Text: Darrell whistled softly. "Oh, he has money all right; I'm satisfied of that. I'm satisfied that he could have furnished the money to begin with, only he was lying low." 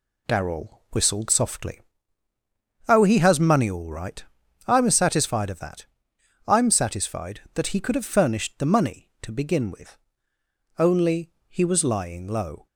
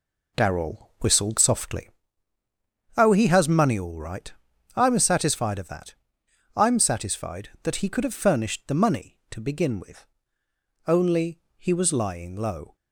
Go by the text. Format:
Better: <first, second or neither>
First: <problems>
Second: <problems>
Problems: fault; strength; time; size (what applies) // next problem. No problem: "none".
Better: first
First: pauses between "only" and "he"; slight; at 11.3 s; 0.18 s long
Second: starts louder than the rest; slight; until 2.0 s; 3 dB // pauses between "only" and "he"; slight; at 11.3 s; 0.18 s long